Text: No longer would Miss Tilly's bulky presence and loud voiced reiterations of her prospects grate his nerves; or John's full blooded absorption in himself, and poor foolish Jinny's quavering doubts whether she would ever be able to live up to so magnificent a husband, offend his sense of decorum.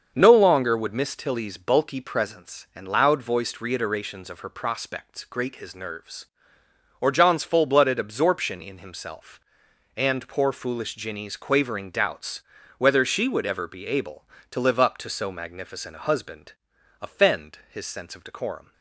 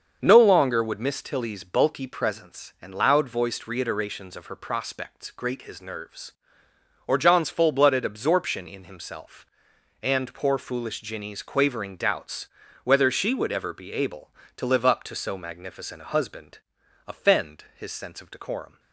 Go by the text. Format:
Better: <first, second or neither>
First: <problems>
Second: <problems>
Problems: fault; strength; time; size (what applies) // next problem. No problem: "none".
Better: neither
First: starts louder than the rest; until 1.1 s; 6.5 dB // pauses between "doubts" and "whether"; slight; at 12.4 s; 0.36 s long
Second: starts louder than the rest; until 1.2 s; 6.5 dB // pauses between "doubts" and "whether"; slight; at 12.4 s; 0.36 s long